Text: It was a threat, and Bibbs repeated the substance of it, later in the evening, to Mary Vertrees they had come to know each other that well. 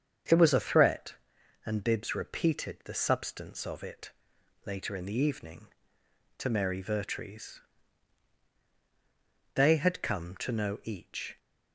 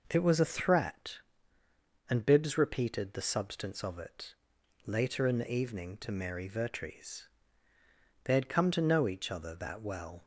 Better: second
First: starts louder than the rest; strong; until 1.7 s; 7 dB // pauses between "Vertrees" and "they"; strong; at 7.6 s; 1.9 s long // stops before "other that well"; at 11.3 s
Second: pauses between "Vertrees" and "they"; noticeable; at 7.2 s; 0.96 s long

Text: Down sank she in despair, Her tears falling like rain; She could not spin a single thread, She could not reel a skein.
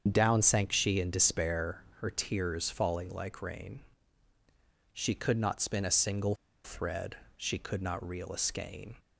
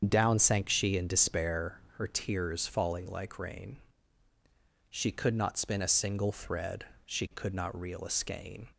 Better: second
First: starts louder than the rest; strong; until 1.1 s; 7 dB // pauses between "single" and "thread"; slight; at 6.3 s; 0.29 s long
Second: starts louder than the rest; strong; until 1.1 s; 7 dB

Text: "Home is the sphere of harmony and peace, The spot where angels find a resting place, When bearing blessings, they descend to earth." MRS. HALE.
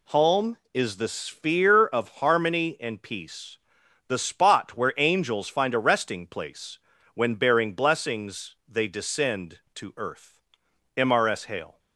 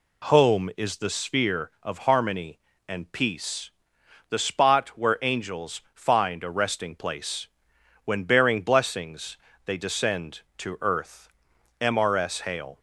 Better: neither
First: none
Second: none

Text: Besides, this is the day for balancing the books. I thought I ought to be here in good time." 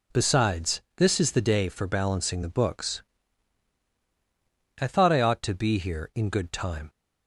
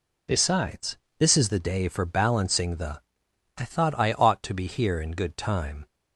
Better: first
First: none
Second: skips "books"; at 3.2 s

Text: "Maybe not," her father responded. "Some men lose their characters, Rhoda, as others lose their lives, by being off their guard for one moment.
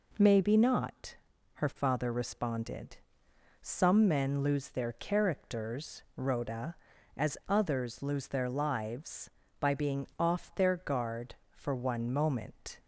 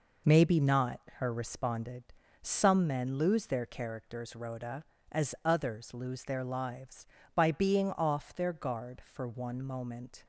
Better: first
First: none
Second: skips "father"; at 1.3 s

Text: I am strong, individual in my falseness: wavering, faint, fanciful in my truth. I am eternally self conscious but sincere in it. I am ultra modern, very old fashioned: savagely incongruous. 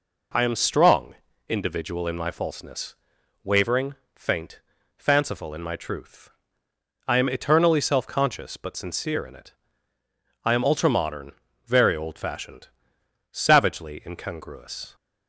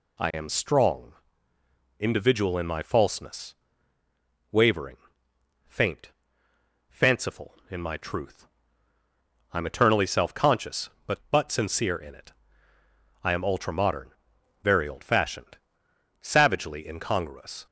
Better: first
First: none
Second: says "but" twice; at 11.2 s

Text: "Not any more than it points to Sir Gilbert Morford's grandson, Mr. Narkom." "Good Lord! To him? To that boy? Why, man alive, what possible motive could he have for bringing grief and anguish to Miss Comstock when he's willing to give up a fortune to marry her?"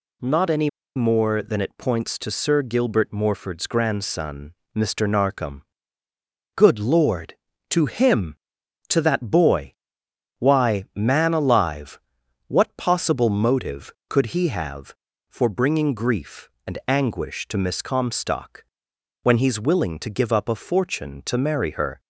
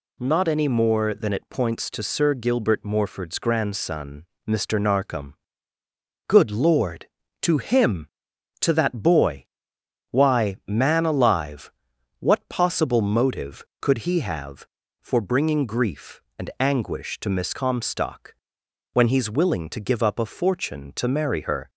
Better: second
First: pauses between "any" and "more"; slight; at 0.6 s; 0.26 s long // pauses between "Comstock" and "when"; noticeable; at 18.6 s; 0.60 s long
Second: pauses between "Comstock" and "when"; noticeable; at 18.3 s; 0.60 s long

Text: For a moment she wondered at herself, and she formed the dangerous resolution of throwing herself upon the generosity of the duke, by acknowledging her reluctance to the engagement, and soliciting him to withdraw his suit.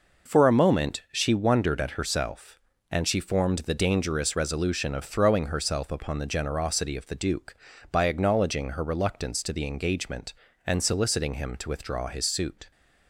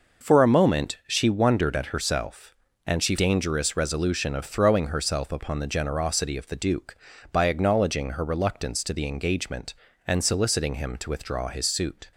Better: first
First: none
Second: skips "formed the"; at 3.1 s

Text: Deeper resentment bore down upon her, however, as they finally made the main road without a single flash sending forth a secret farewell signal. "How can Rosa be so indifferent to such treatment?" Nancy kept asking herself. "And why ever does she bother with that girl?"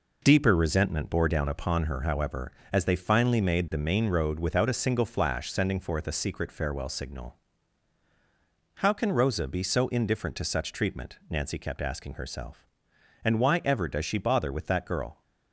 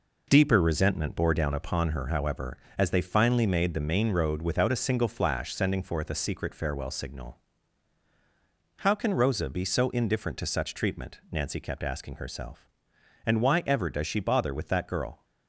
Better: neither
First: none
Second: none

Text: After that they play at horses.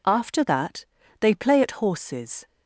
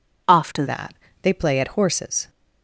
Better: first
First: pauses between "that" and "they"; slight; at 0.8 s; 0.34 s long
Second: changes voice at "that"; from 0.6 s on; 1.6 s long // pauses between "that" and "they"; slight; at 0.9 s; 0.28 s long

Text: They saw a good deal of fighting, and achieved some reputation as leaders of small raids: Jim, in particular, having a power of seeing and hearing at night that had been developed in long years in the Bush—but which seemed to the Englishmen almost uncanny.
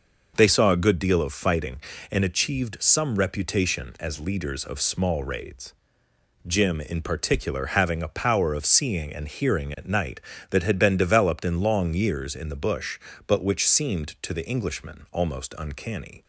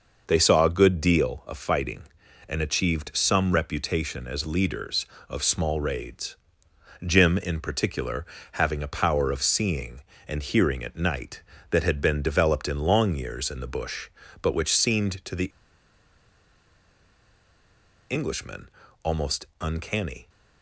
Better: first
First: none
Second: pauses between "the" and "Englishmen"; strong; at 15.4 s; 2.6 s long // pauses between "Englishmen" and "almost"; slight; at 18.6 s; 0.34 s long

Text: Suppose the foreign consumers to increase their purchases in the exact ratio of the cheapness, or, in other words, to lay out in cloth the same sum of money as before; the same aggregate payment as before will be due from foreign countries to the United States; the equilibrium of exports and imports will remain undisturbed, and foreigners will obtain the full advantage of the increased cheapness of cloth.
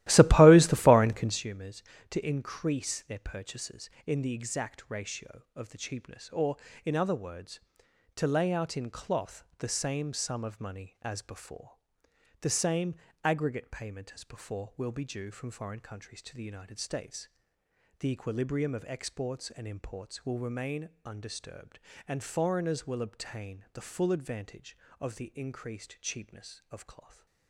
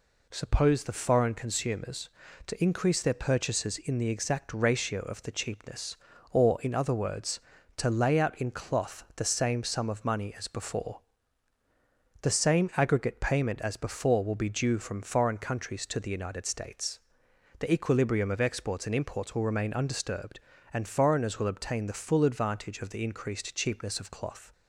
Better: second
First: starts louder than the rest; strong; until 1.5 s; 15.5 dB // pauses between "same" and "aggregate"; slight; at 12.9 s; 0.26 s long // pauses between "remain" and "undisturbed"; slight; at 20.8 s; 0.16 s long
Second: none

